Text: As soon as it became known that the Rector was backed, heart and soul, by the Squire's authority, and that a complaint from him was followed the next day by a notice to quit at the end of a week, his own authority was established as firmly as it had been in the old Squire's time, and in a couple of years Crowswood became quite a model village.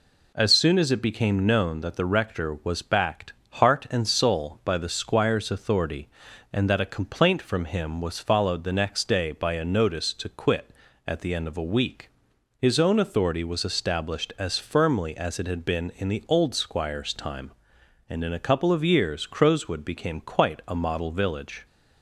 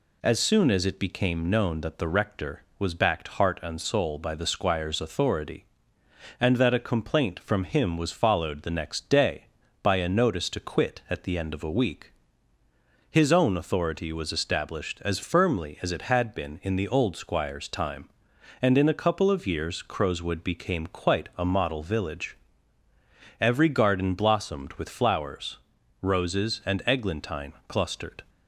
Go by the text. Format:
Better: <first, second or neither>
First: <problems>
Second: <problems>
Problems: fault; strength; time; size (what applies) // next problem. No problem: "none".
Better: first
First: none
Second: goes on to say "Every garden blossomed with flowers roses and eglantine clustered"; strong; from 23.3 s on; 4.8 s long